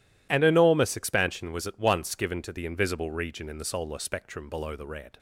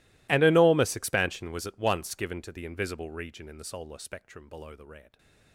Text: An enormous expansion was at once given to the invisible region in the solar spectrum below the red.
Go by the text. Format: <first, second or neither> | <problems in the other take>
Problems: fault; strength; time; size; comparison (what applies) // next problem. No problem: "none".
first | gets quieter; strong; throughout; 27.5 dB